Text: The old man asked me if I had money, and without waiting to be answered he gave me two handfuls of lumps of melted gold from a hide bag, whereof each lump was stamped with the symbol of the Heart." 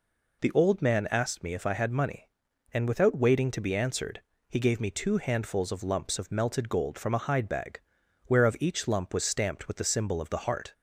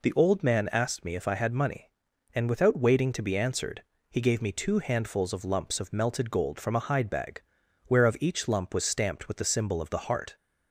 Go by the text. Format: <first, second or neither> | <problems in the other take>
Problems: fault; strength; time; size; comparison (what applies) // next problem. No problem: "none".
neither | pauses between "answered" and "he"; slight; the same in both